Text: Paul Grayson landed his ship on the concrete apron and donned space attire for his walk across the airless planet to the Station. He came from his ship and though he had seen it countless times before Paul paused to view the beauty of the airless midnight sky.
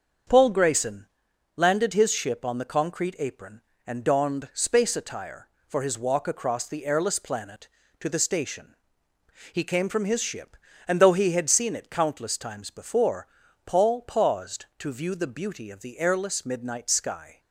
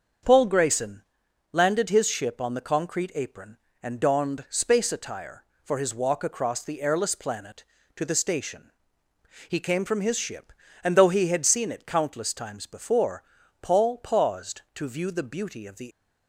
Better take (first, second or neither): first